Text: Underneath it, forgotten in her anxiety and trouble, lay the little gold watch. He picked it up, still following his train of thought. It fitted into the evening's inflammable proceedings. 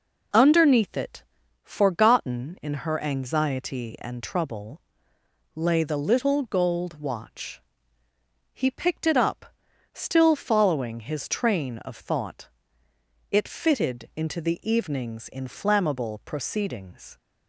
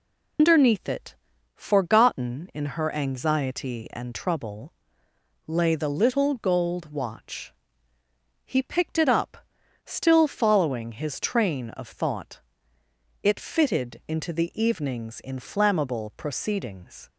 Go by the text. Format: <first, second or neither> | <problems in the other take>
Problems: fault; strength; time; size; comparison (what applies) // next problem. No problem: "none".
first | loses the start of "Underneath"; at 0.3 s; 145 ms